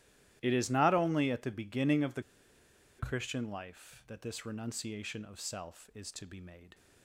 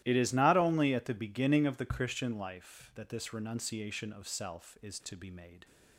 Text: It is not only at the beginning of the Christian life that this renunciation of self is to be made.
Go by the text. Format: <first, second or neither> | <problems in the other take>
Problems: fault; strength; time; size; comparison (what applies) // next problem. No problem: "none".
second | starts louder than the rest; strong; until 1.4 s; 14 dB; strong in the second // pauses between "the" and "Christian"; noticeable; at 2.2 s; 0.76 s long